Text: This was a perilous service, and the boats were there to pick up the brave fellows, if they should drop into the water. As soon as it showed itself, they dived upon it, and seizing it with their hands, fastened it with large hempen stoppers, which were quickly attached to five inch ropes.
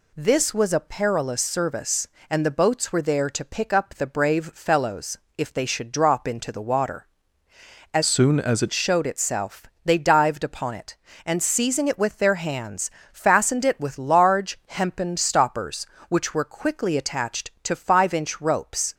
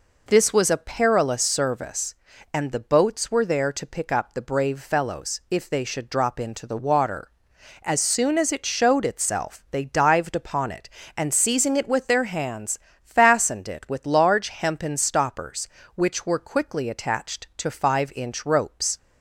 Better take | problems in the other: second | changes voice from "soon" to "it"; from 8.0 to 8.7 s; 0.7 s long

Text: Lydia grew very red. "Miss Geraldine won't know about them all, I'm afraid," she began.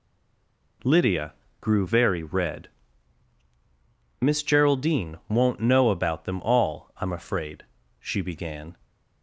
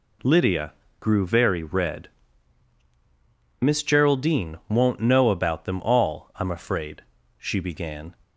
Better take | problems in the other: second | stays silent before the first word; slight; until 0.8 s; 0.8 s long // pauses between "Lydia" and "grew"; slight; at 1.3 s; 0.26 s long; slight in the second

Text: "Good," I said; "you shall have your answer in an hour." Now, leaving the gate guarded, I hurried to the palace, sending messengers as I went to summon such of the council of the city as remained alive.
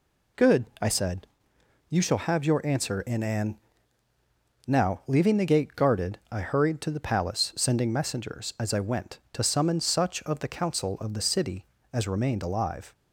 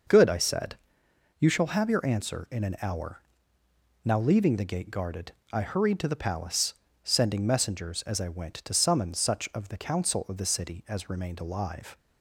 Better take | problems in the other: second | skips "hour"; at 4.1 s

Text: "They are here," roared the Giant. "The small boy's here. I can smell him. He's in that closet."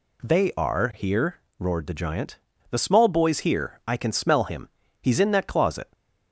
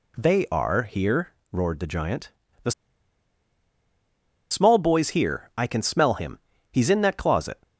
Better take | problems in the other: first | pauses between "The" and "small"; strong; at 2.7 s; 1.7 s long

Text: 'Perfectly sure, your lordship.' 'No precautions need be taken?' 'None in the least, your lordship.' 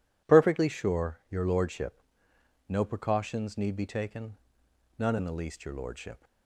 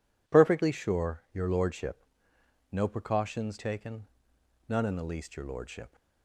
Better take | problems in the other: first | skips "need be"; at 3.5 s

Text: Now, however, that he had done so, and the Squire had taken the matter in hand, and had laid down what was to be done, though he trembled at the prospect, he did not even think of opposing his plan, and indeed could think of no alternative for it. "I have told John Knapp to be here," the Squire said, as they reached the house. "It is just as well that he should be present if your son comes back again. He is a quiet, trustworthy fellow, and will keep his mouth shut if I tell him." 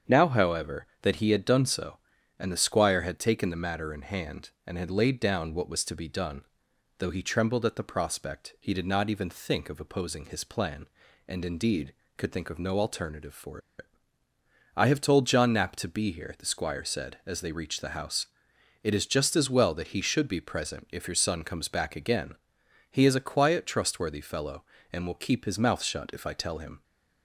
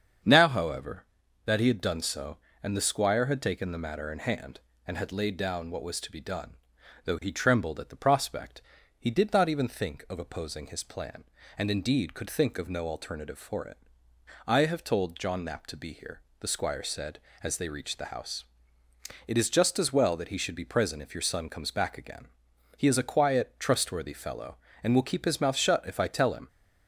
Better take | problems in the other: second | starts louder than the rest; strong; until 1.2 s; 7 dB; strong in the second // pauses between "for" and "it"; slight; at 13.5 s; 0.19 s long

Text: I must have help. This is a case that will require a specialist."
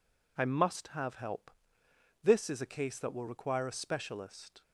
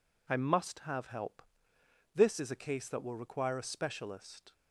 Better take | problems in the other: neither | none

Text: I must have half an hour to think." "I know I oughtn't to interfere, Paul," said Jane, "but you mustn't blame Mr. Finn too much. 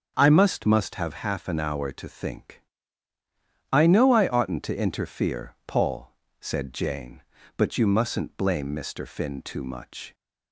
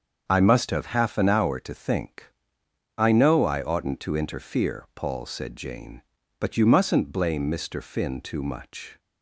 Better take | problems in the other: second | starts louder than the rest; until 1.1 s; 7 dB; also in the second // says "must" twice; at 0.6 s

